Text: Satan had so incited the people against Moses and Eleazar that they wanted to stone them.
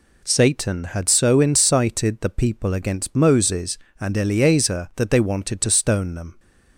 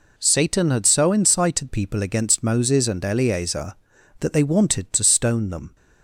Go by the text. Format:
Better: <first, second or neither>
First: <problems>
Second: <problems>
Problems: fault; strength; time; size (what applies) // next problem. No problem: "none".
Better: first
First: none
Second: skips "the"; at 1.6 s